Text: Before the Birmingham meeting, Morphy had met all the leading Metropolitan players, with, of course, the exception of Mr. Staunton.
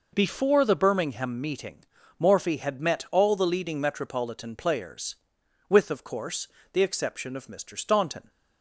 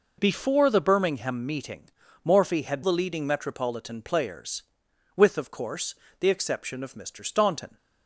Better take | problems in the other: first | skips "met all"; at 2.8 s

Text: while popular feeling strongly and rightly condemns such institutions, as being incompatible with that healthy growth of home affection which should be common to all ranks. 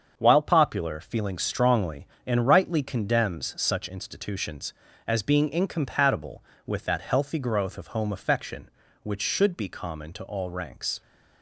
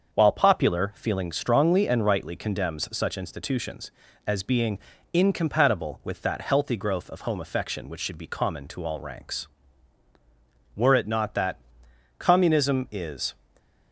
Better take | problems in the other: first | starts louder than the rest; until 1.1 s; 6.5 dB; also in the first // pauses between "being" and "incompatible"; slight; at 4.7 s; 0.36 s long // goes on to say "Were it not that Communism is"; strong; from 10.7 s on; 2.5 s long // stays silent after the last word; slight; from 13.3 s on; 0.6 s long

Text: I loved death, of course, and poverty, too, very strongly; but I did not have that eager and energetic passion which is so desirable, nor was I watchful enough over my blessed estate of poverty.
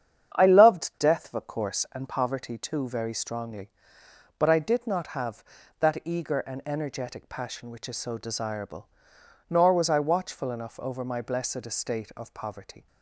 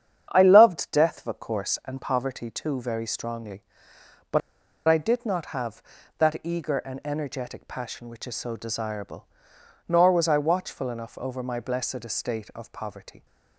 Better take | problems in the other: first | starts louder than the rest; strong; until 1.3 s; 8.5 dB; strong in the first // pauses between "but" and "I"; noticeable; at 4.4 s; 0.48 s long

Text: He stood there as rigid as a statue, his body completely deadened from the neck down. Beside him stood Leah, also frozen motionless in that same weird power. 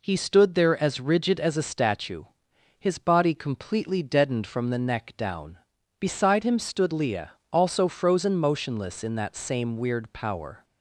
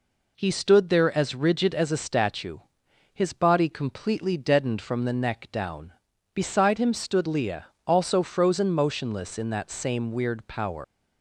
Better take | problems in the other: first | leaves "power" unfinished; at 10.8 s; 145 ms

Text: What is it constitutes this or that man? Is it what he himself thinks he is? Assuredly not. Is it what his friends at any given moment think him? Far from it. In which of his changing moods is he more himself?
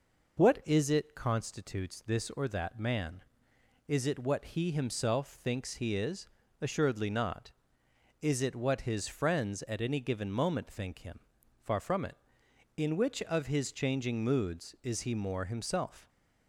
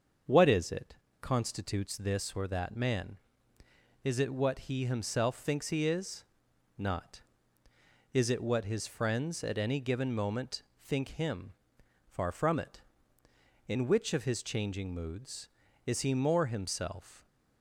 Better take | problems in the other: first | starts louder than the rest; until 1.5 s; 6.5 dB // pauses between "it" and "constitutes"; slight; at 0.9 s; 0.26 s long // skips "Assuredly"; at 6.5 s // pauses between "moment" and "think"; slight; at 10.6 s; 0.20 s long

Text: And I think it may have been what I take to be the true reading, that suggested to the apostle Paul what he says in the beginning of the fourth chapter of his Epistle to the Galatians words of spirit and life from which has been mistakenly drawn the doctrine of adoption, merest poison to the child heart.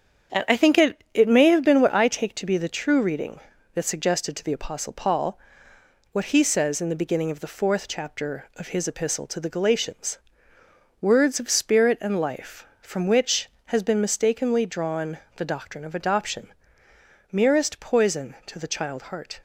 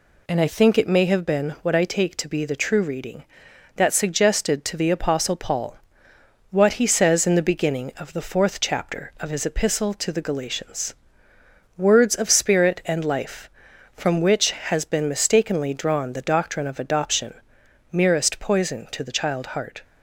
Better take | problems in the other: second | starts louder than the rest; strong; until 1.4 s; 7.5 dB // says "it" twice; at 1.1 s // pauses between "Paul" and "what"; noticeable; at 5.3 s; 0.76 s long; noticeable in the second // pauses between "Galatians" and "words"; noticeable; at 10.1 s; 0.82 s long; noticeable in the second // pauses between "drawn" and "the"; slight; at 15.1 s; 0.20 s long

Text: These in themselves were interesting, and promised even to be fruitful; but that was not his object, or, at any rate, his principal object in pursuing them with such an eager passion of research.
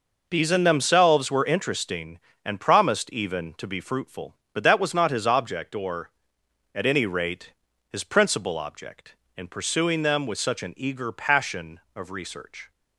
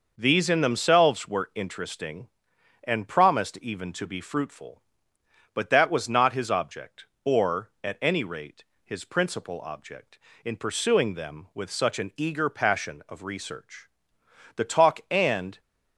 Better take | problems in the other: first | goes on to say "The talk and"; noticeable; from 14.5 s on; 1.0 s long

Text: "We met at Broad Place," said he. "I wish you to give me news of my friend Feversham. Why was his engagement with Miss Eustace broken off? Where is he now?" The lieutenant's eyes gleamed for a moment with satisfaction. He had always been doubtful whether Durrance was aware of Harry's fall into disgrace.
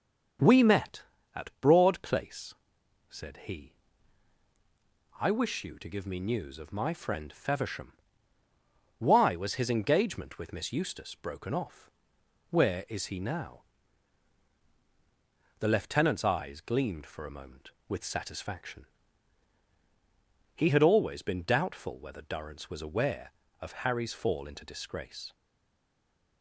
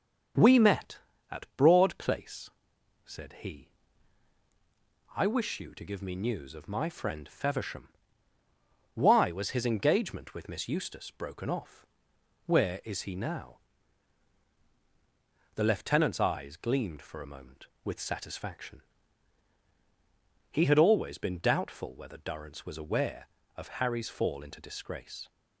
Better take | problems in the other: second | starts louder than the rest; until 1.8 s; 7 dB; also in the second // stays silent after the last word; from 25.3 s on; 1.1 s long

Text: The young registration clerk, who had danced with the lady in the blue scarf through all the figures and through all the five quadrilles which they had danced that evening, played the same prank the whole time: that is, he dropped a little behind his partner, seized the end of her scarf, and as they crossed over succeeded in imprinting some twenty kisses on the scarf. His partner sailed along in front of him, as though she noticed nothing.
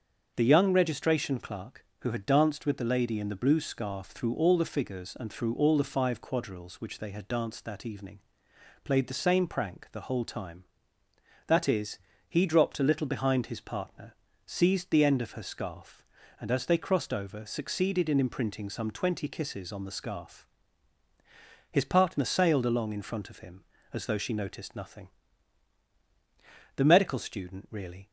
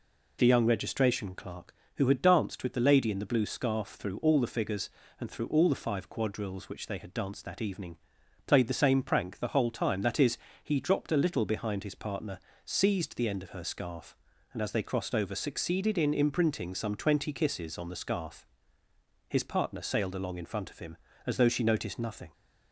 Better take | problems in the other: second | starts louder than the rest; strong; until 1.3 s; 7 dB // goes on to say "The medical student really"; from 26.7 s on; 1.3 s long

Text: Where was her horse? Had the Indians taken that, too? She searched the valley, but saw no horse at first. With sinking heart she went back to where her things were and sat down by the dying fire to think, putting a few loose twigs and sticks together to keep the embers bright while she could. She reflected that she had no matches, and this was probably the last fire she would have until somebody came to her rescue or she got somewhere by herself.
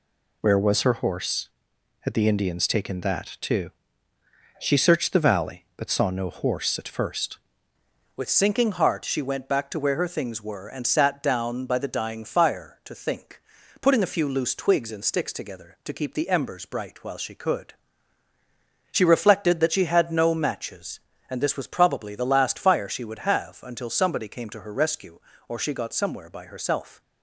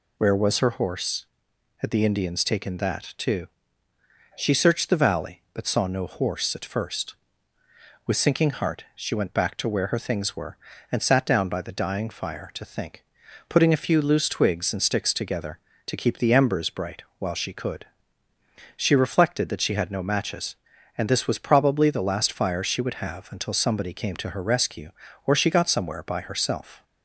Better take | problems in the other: second | changes voice at "With"; from 8.1 s on; 18.9 s long

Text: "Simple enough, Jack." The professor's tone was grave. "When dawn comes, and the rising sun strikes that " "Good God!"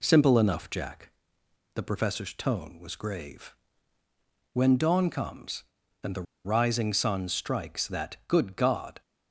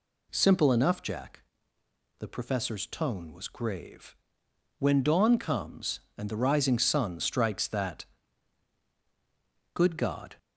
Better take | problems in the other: second | pauses between "the" and "rising"; slight; at 6.2 s; 0.20 s long

